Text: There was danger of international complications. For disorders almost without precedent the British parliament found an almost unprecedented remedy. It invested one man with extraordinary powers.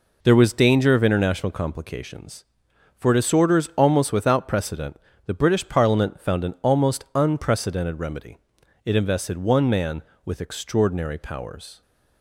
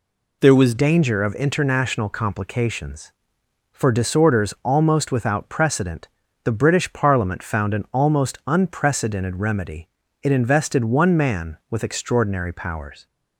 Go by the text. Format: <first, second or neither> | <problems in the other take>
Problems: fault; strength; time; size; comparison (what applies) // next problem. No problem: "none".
first | changes voice at "danger"; from 0.7 s on; 12.3 s long // pauses between "precedent" and "the"; slight; at 6.0 s; 0.36 s long; slight in the first